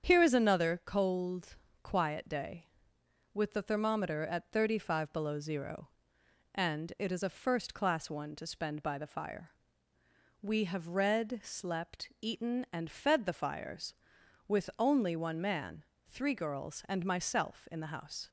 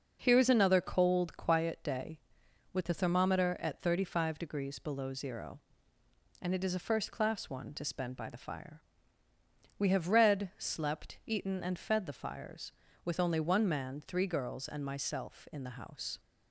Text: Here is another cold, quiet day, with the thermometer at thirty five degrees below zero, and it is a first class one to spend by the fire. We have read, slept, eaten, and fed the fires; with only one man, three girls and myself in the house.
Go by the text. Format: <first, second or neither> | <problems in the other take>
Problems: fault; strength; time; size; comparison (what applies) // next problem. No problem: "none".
second | starts louder than the rest; strong; until 1.0 s; 8 dB // skips "degrees"; at 5.1 s